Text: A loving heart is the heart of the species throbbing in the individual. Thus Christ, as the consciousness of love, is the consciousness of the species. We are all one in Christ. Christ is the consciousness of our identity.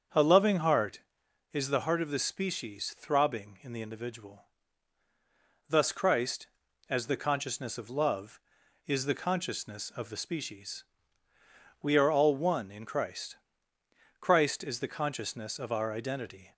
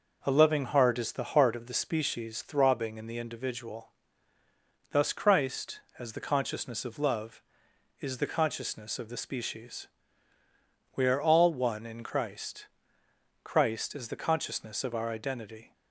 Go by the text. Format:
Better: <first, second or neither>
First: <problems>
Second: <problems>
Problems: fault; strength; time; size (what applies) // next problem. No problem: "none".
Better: second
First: starts louder than the rest; strong; until 1.4 s; 7 dB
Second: none